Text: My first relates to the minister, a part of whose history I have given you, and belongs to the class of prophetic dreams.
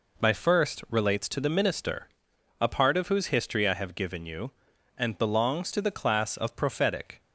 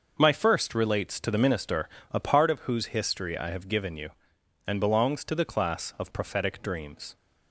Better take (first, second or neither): second